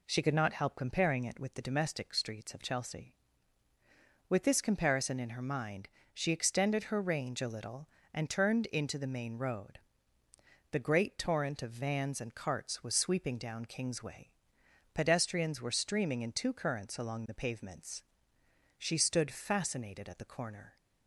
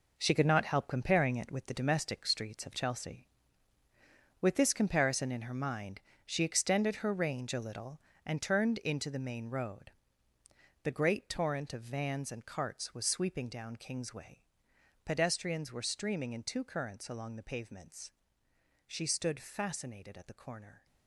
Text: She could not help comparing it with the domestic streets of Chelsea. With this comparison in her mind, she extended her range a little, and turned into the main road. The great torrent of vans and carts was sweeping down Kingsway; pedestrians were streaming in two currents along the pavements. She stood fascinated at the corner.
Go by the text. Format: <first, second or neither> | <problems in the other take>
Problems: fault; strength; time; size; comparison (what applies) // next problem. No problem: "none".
first | gets quieter; strong; throughout; 10 dB